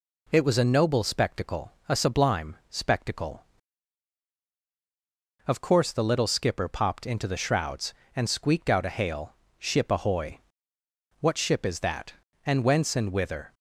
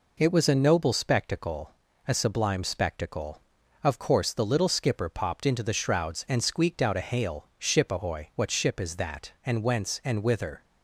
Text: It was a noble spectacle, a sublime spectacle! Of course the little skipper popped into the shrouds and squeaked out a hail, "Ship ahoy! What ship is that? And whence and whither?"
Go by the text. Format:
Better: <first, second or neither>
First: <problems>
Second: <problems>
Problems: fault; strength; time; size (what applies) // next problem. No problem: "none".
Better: neither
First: none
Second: none